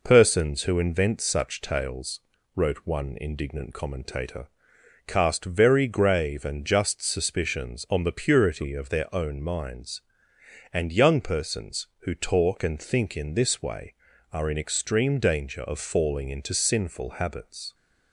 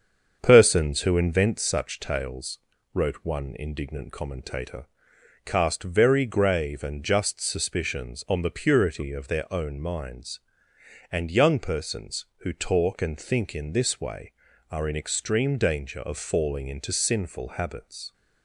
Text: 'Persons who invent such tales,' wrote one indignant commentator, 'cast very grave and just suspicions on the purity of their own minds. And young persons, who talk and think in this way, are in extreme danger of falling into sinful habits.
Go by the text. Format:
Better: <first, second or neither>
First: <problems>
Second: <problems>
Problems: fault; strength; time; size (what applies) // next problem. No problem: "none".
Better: first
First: none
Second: starts louder than the rest; strong; until 1.7 s; 7 dB